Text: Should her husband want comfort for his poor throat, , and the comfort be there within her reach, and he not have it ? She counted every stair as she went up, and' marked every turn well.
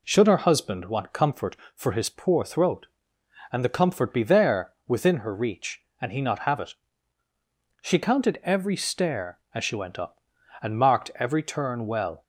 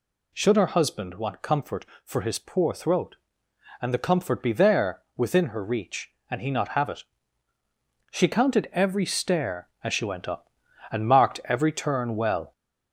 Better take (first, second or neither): first